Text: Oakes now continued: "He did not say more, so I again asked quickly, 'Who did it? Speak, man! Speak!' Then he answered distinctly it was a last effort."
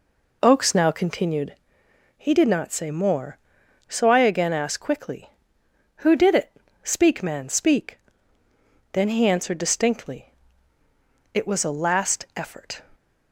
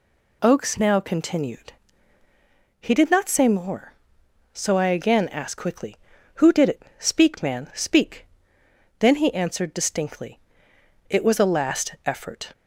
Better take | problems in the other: second | starts louder than the rest; until 1.4 s; 3.5 dB // pauses between "distinctly" and "it"; at 10.2 s; 1.0 s long; noticeable in the second

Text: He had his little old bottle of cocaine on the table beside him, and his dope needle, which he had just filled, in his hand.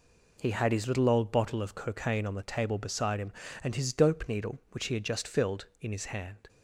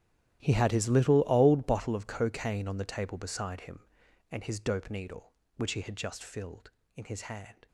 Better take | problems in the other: first | gets quieter; strong; throughout; 18.5 dB

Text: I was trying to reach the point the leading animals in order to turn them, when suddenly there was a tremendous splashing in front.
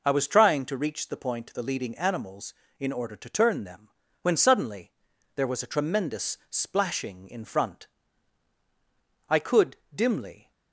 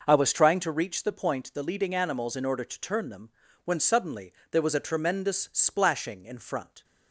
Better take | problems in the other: second | pauses between "suddenly" and "there"; at 4.9 s; 0.44 s long; slight in the second // goes on to say "I could dimly"; noticeable; from 9.2 s on; 1.2 s long

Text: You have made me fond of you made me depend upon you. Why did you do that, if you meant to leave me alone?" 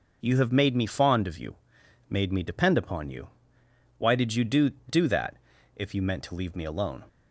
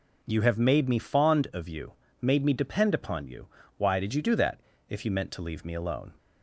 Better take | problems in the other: second | pauses between "you" and "made"; noticeable; at 1.5 s; 0.52 s long; slight in the second // says "do" twice; at 4.8 s

